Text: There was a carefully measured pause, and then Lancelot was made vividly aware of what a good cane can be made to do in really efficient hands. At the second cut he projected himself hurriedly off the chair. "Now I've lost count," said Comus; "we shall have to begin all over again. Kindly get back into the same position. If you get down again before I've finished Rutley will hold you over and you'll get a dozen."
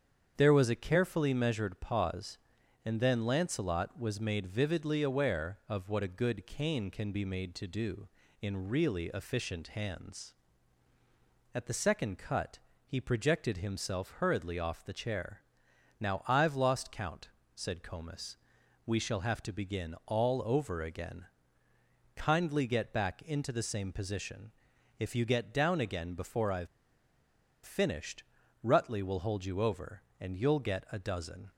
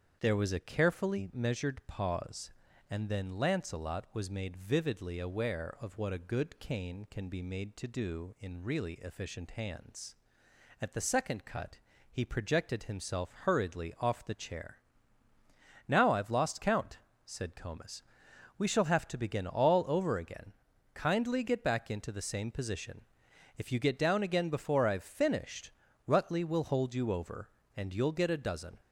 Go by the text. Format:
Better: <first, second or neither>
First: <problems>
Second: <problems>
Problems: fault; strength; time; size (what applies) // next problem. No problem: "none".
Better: second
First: starts louder than the rest; strong; until 1.3 s; 8 dB // pauses between "cut" and "he"; slight; at 12.5 s; 0.26 s long // pauses between "I've" and "finished"; at 26.6 s; 0.98 s long // pauses between "finished" and "Rutley"; at 28.2 s; 0.40 s long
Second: starts louder than the rest; strong; until 1.2 s; 7.5 dB // pauses between "cut" and "he"; slight; at 11.7 s; 0.32 s long // pauses between "finished" and "Rutley"; slight; at 25.6 s; 0.36 s long